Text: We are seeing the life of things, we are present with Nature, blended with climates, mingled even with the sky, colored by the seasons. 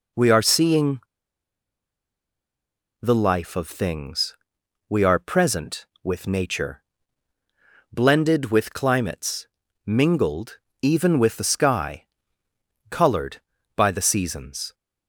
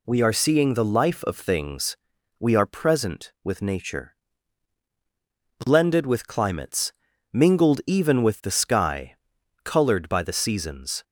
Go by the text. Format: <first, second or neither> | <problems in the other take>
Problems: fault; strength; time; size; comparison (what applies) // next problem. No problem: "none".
second | pauses between "seeing" and "the"; strong; at 0.9 s; 2.0 s long // pauses between "mingled" and "even"; slight; at 10.5 s; 0.22 s long